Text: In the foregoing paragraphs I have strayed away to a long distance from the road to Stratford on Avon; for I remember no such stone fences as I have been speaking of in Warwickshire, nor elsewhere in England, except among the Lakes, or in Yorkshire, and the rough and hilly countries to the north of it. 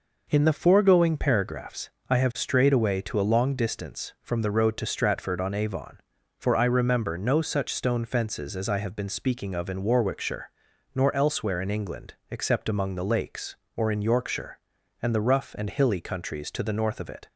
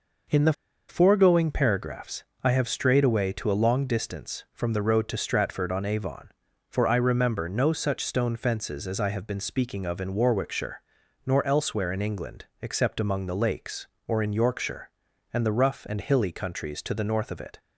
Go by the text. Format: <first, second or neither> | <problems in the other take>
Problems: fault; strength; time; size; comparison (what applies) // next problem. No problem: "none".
first | pauses between "the" and "foregoing"; at 0.5 s; 0.36 s long // pauses between "paragraphs" and "I"; slight; at 2.2 s; 0.22 s long; slight in the first